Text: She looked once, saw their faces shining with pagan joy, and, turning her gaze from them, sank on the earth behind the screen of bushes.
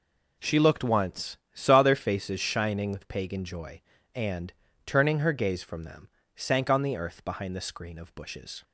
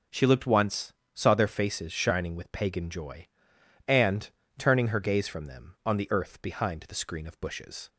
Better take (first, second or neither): first